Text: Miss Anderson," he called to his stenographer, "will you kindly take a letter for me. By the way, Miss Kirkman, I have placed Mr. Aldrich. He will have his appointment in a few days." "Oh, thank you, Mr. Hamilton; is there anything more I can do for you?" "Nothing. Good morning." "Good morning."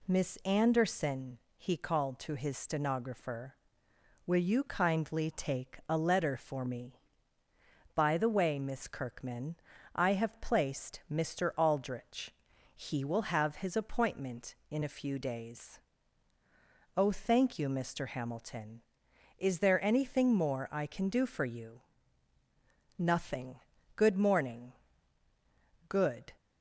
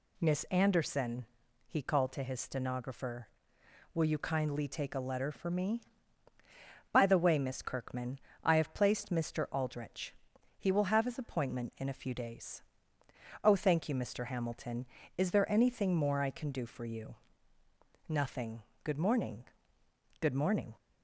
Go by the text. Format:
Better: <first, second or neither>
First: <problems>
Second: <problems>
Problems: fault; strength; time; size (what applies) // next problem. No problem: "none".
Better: second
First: stops before "morning"; at 26.3 s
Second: none